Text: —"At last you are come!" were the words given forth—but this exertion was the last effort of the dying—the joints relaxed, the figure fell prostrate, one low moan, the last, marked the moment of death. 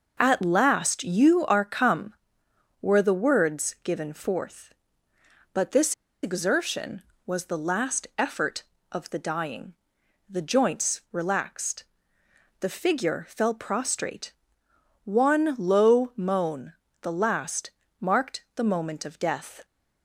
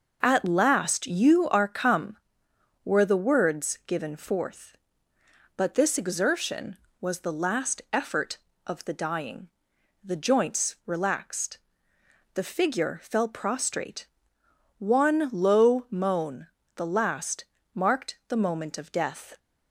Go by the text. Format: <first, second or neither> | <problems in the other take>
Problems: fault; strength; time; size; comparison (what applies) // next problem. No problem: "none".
second | pauses between "this" and "exertion"; slight; at 5.9 s; 0.28 s long